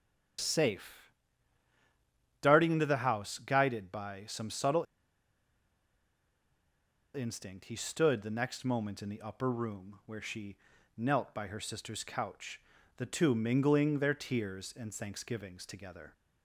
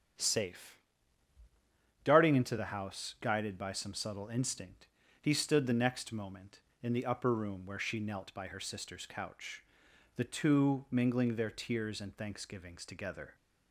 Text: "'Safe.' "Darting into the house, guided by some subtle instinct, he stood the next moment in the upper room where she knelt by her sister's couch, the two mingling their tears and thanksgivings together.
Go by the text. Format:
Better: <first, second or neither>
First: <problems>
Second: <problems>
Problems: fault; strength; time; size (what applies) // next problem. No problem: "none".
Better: second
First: starts louder than the rest; strong; until 2.7 s; 8.5 dB // pauses between "subtle" and "instinct"; strong; at 4.8 s; 2.3 s long // pauses between "she" and "knelt"; at 10.5 s; 0.38 s long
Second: starts louder than the rest; strong; until 2.4 s; 8.5 dB